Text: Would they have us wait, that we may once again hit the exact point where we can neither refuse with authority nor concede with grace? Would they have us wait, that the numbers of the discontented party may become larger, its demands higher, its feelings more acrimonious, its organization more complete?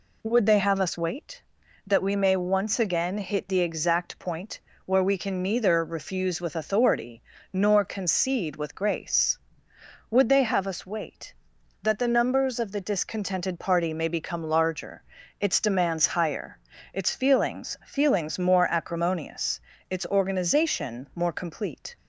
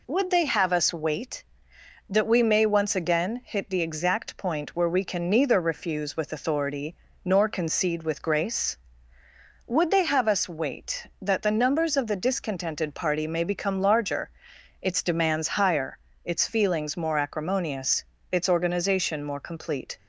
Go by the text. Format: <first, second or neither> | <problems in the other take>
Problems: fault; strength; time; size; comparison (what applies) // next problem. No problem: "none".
second | pauses between "point" and "where"; slight; at 4.6 s; 0.24 s long // pauses between "authority" and "nor"; slight; at 7.2 s; 0.32 s long; slight in the second // says "feelings" twice; at 17.8 s